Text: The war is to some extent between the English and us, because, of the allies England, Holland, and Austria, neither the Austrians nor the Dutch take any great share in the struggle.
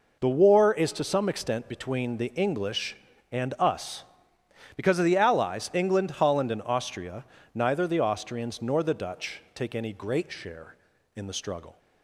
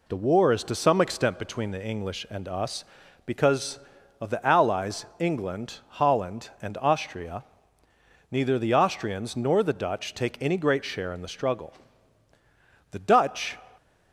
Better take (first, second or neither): first